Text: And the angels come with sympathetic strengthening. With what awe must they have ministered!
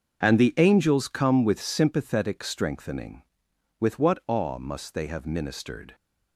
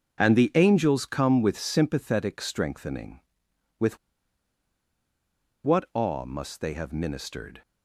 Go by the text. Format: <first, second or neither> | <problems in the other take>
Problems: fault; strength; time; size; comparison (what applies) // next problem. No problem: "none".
first | starts louder than the rest; until 1.2 s; 6.5 dB; also in the first // pauses between "With" and "what"; strong; at 3.9 s; 1.6 s long